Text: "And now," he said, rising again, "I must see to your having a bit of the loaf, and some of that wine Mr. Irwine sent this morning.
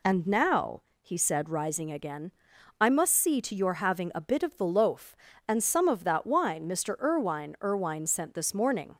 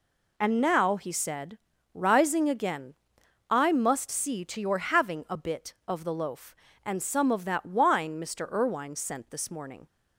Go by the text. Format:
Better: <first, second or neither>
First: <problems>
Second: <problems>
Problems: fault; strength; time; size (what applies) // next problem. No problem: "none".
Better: second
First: says "Irwine" twice; at 7.6 s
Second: none